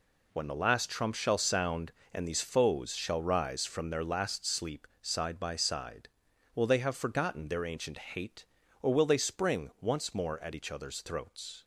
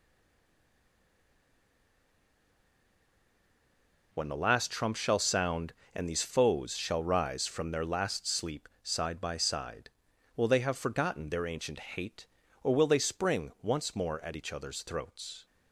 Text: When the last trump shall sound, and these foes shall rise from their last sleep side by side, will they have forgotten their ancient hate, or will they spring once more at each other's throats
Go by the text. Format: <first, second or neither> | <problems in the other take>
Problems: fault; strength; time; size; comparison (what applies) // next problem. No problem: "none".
first | stays silent before the first word; strong; until 4.1 s; 4.1 s long // pauses between "sleep" and "side"; slight; at 8.6 s; 0.16 s long; slight in the first